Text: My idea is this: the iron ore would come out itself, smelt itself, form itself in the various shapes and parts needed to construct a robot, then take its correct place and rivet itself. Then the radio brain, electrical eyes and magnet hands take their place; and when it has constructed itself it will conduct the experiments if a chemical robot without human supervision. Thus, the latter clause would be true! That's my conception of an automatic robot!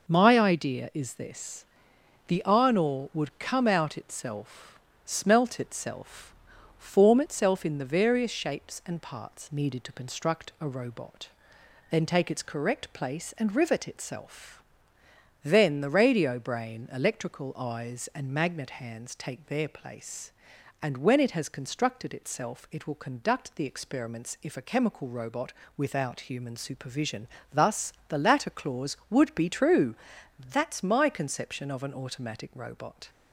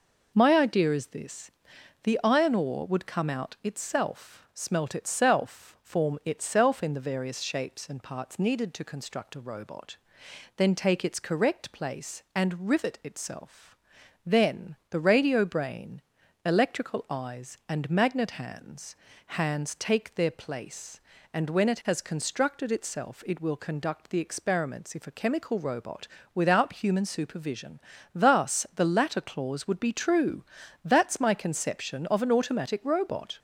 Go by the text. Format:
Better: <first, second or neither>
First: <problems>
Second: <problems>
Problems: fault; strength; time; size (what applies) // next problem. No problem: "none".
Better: first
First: pauses between "robot" and "without"; slight; at 25.5 s; 0.24 s long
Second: says "hands" twice; at 19.2 s // pauses between "robot" and "without"; slight; at 26.0 s; 0.28 s long